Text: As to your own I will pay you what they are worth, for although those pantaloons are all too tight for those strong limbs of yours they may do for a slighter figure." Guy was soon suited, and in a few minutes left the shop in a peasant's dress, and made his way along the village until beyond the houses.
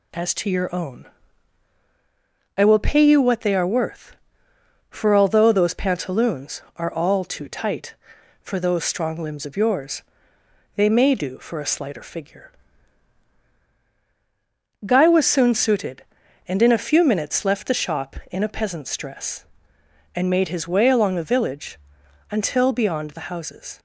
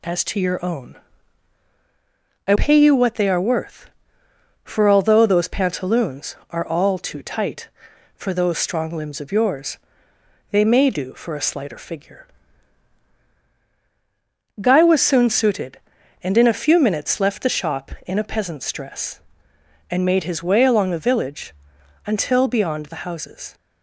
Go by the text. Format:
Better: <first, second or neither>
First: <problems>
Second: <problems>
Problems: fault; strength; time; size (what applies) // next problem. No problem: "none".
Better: first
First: pauses between "own" and "I"; strong; at 1.0 s; 1.5 s long // pauses between "yours" and "they"; noticeable; at 10.0 s; 0.74 s long // pauses between "village" and "until"; noticeable; at 21.7 s; 0.50 s long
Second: pauses between "own" and "I"; strong; at 0.9 s; 1.5 s long // skips "will"; at 2.5 s // pauses between "yours" and "they"; noticeable; at 9.7 s; 0.74 s long // pauses between "village" and "until"; noticeable; at 21.5 s; 0.50 s long